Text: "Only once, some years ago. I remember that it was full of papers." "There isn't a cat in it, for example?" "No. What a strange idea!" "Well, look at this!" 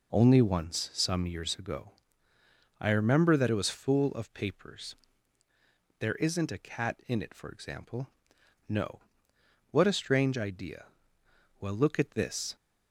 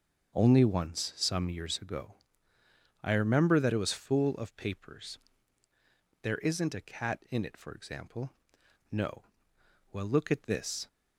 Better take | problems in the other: first | starts louder than the rest; until 1.3 s; 6.5 dB // skips "What a strange idea"; at 9.5 s

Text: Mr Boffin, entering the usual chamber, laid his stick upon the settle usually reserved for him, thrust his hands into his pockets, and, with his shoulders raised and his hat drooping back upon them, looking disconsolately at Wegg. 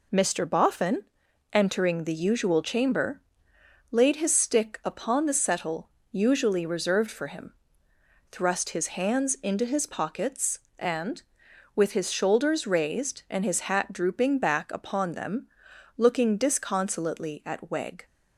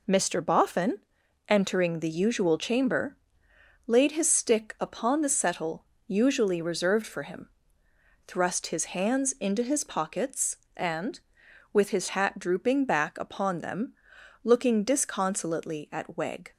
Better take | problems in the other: first | pauses between "settle" and "usually"; slight; at 5.8 s; 0.22 s long; slight in the first // skips "shoulders raised and his"; at 12.0 s

